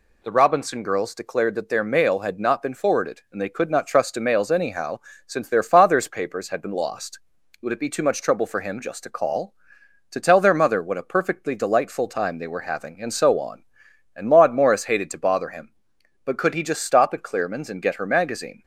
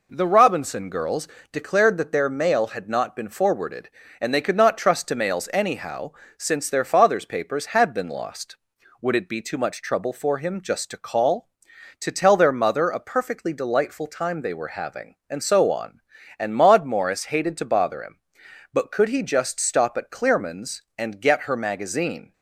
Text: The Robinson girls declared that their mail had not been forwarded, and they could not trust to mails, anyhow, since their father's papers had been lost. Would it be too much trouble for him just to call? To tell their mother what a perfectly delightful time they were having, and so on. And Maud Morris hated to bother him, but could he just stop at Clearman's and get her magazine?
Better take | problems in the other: first | pauses between "girls" and "declared"; slight; at 1.2 s; 0.24 s long // skips "what"; at 12.8 s

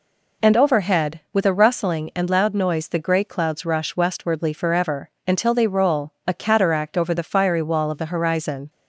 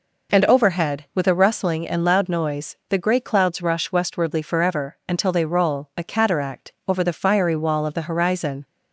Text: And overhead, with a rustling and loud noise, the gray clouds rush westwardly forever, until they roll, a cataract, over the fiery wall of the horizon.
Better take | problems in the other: neither | none

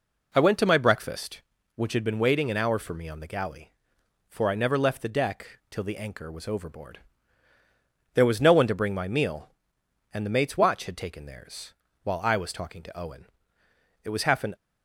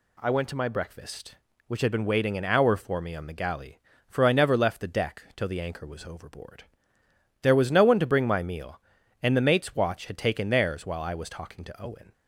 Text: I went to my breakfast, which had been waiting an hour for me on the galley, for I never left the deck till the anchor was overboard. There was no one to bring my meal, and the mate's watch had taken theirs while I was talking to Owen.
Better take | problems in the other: second | pauses between "theirs" and "while"; slight; at 11.7 s; 0.30 s long // goes on to say "It was half an"; from 13.9 s on; 0.56 s long

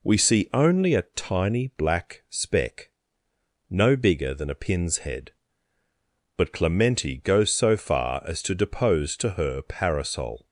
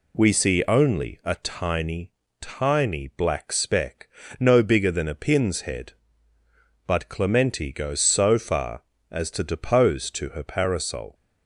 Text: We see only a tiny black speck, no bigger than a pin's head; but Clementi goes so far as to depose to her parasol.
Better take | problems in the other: first | says "tiny" twice; at 2.4 s

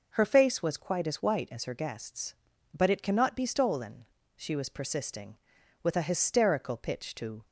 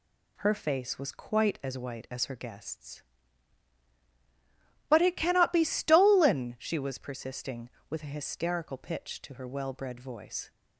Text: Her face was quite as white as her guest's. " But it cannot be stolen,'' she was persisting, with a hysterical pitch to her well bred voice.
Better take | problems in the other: second | stops before "her well bred voice"; at 7.4 s

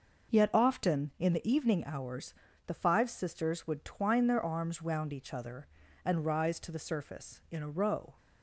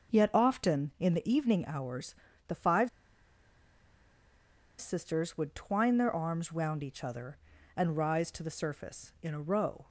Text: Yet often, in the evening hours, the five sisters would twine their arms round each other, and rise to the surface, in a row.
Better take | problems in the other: first | pauses between "five" and "sisters"; strong; at 2.8 s; 1.9 s long

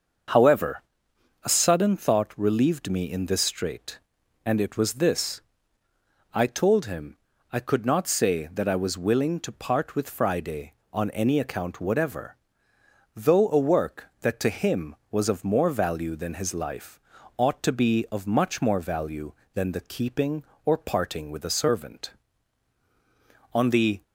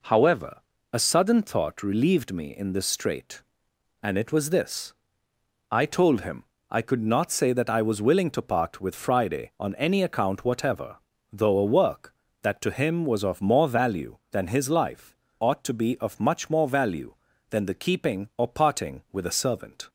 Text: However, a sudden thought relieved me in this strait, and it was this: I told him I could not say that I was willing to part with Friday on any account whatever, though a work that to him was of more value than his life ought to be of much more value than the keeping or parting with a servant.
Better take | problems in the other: second | starts louder than the rest; until 1.9 s; 6.5 dB // pauses between "him" and "I"; slight; at 7.1 s; 0.34 s long; slight in the second // pauses between "life" and "ought"; at 16.9 s; 0.40 s long; slight in the second // goes on to say "On the"; slight; from 23.5 s on; 0.48 s long

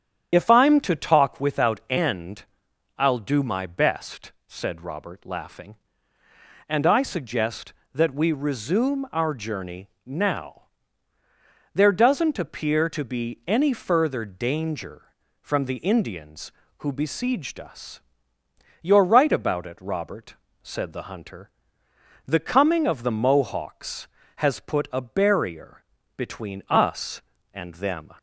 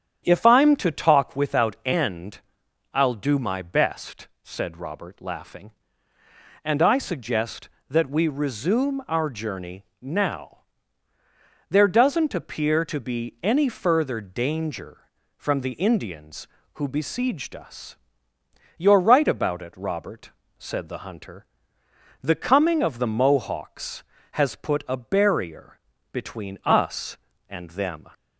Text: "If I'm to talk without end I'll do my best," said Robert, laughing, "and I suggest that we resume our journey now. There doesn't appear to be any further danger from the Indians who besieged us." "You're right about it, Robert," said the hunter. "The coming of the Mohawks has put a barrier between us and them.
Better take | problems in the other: second | loses the start of "If"; at 0.3 s; 45 ms // starts louder than the rest; strong; until 1.3 s; 9 dB; strong in the second // pauses between "end" and "I'll"; noticeable; at 2.4 s; 0.54 s long; noticeable in the second // pauses between "journey" and "now"; slight; at 9.8 s; 0.16 s long; slight in the second // pauses between "barrier" and "between"; slight; at 25.8 s; 0.32 s long; slight in the second

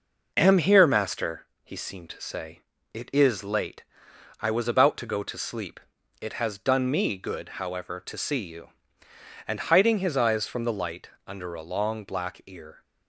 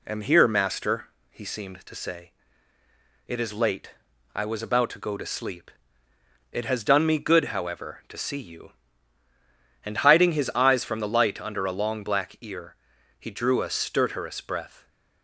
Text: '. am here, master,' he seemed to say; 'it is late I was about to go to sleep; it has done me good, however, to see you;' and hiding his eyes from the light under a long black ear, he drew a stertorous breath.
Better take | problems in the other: second | pauses between "late" and "I"; noticeable; at 3.8 s; 0.58 s long; also in the second // pauses between "light" and "under"; slight; at 11.1 s; 0.16 s long // stops before "he drew a stertorous breath"; at 12.8 s

